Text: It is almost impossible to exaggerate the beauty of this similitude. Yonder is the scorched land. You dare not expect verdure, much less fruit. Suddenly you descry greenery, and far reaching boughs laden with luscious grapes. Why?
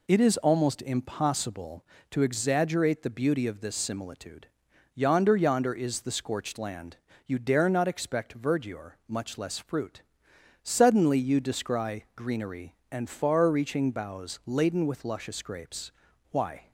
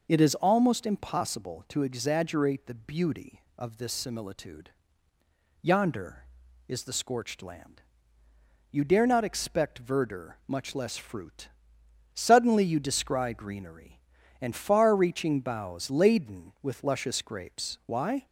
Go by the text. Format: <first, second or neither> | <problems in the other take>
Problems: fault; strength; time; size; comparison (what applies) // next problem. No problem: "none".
second | says "Yonder" twice; at 5.3 s